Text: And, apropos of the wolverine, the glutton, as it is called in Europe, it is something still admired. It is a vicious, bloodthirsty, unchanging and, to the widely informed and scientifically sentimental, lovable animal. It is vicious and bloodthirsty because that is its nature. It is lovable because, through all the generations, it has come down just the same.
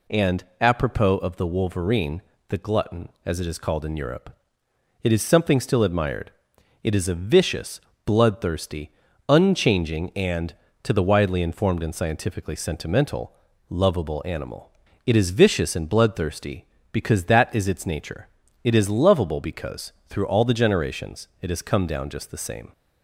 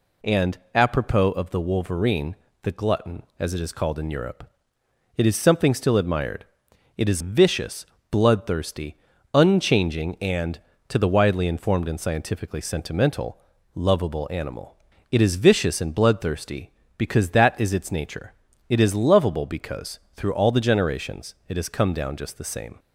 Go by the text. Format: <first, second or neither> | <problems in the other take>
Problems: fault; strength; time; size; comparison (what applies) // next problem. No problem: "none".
first | skips "a"; at 7.2 s